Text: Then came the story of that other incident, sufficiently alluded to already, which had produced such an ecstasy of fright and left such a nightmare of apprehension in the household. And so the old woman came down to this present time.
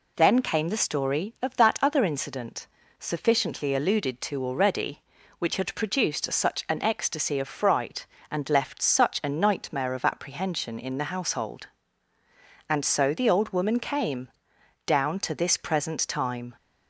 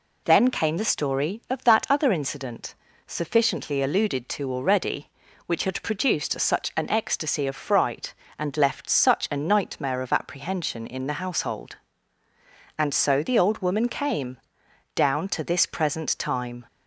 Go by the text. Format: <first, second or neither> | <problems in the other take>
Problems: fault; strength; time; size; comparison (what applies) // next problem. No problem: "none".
neither | pauses between "came" and "down"; noticeable; the same in both